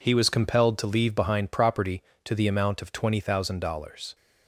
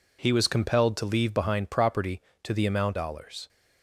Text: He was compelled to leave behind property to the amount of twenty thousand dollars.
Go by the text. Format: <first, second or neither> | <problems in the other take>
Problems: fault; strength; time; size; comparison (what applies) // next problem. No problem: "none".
first | skips "of twenty thousand"; at 2.9 s